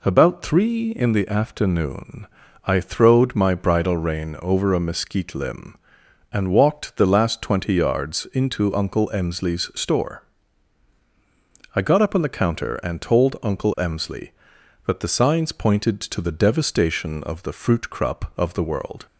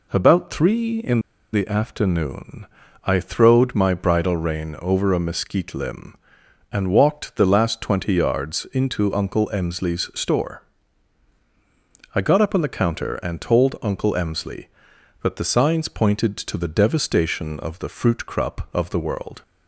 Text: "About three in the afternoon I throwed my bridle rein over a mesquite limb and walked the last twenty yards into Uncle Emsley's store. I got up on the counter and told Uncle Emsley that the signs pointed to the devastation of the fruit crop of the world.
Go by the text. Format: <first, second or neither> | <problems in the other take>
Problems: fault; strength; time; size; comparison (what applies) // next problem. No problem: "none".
first | pauses between "in" and "the"; slight; at 1.2 s; 0.32 s long // pauses between "afternoon" and "I"; at 2.6 s; 0.38 s long; also in the first